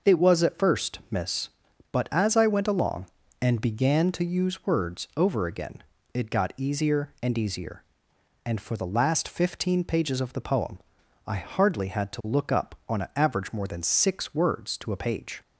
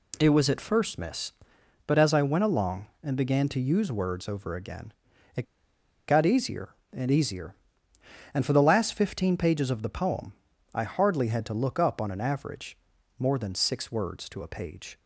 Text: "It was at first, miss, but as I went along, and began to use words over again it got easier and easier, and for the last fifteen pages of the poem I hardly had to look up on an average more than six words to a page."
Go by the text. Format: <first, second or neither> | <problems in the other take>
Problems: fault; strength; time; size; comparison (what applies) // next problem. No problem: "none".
first | pauses between "again" and "it"; at 4.9 s; 0.44 s long; slight in the first // pauses between "it" and "got"; noticeable; at 5.4 s; 0.64 s long // pauses between "poem" and "I"; at 10.3 s; 0.42 s long; noticeable in the first // pauses between "average" and "more"; at 12.7 s; 0.40 s long